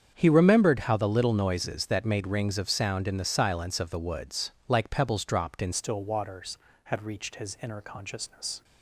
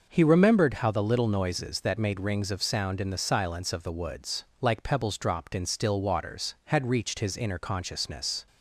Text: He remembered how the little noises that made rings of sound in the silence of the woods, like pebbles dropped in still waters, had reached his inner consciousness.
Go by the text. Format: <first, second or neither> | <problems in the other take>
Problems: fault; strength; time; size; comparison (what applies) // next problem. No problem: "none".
second | starts louder than the rest; strong; until 1.1 s; 7.5 dB // changes voice at "still"; from 5.7 s on; 2.9 s long